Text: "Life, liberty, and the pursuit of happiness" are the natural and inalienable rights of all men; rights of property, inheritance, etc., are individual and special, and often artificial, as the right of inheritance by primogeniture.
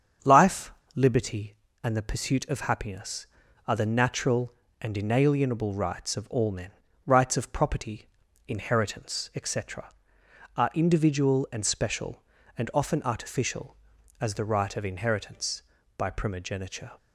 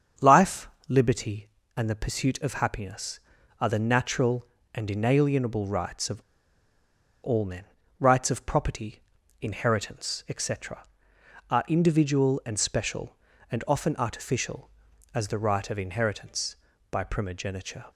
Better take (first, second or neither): first